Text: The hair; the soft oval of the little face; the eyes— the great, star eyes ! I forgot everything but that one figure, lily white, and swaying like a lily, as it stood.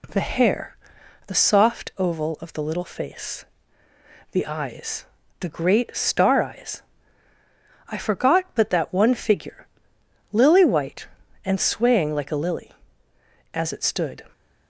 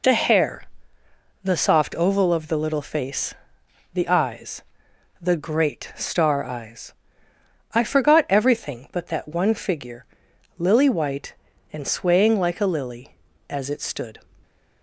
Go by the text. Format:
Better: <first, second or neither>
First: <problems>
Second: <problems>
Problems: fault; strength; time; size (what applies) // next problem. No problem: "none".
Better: second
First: skips "everything"; at 8.4 s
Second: none